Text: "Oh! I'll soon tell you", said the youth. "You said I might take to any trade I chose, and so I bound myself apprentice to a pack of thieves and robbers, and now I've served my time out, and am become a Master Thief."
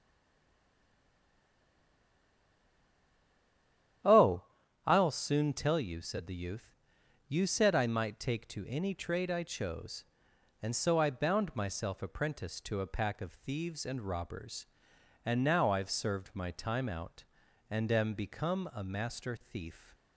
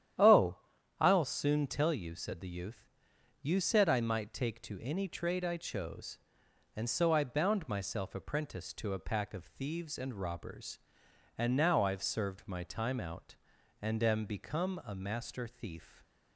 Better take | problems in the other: second | stays silent before the first word; strong; until 4.0 s; 4.0 s long // starts louder than the rest; strong; until 5.4 s; 10.5 dB; strong in the second

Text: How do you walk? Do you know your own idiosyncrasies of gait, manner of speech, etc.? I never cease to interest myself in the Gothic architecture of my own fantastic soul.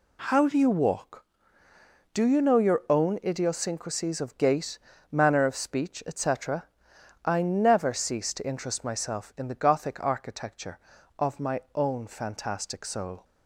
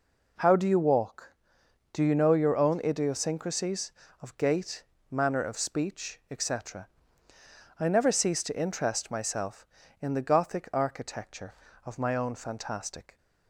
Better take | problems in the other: first | stops before "soul"; at 13.1 s

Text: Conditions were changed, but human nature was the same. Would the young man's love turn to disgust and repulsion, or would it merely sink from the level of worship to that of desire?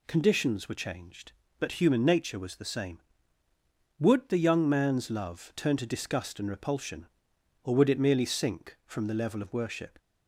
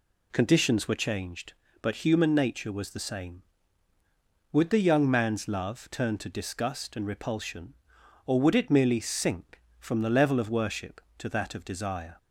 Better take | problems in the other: second | stops before "to that of desire"; at 9.9 s

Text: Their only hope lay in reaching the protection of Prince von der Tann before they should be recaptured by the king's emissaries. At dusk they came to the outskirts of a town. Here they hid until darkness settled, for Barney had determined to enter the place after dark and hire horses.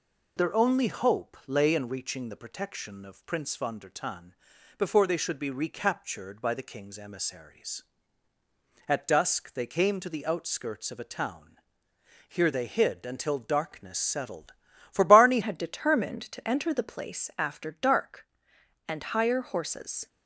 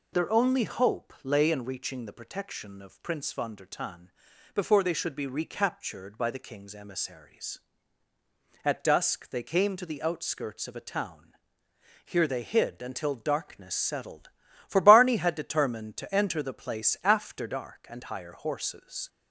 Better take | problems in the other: second | pauses between "Tann" and "before"; at 4.3 s; 0.42 s long; also in the second // changes voice at "had"; from 15.4 s on; 4.6 s long

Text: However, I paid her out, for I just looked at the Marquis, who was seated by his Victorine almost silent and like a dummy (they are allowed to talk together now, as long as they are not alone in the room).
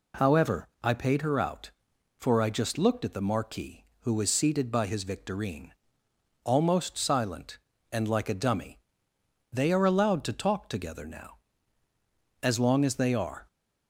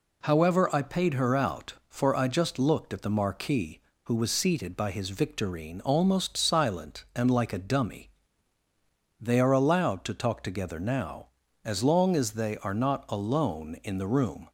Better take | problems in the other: second | pauses between "Victorine" and "almost"; noticeable; at 5.7 s; 0.74 s long // stops before "not alone in the room"; at 13.4 s

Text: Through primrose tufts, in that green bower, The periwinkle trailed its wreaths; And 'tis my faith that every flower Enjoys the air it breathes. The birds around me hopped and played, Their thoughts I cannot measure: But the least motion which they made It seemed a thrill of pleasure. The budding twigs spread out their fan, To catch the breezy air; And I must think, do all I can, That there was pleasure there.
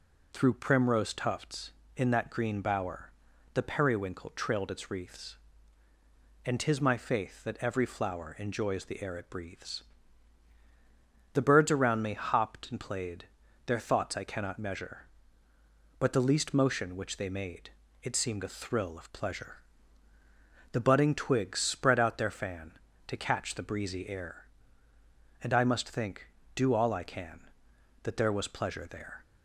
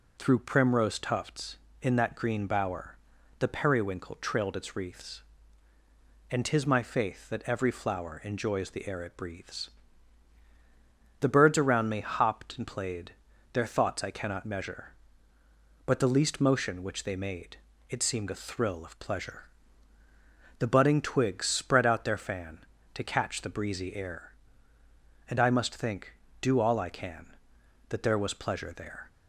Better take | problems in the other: neither | pauses between "made" and "It"; slight; the same in both

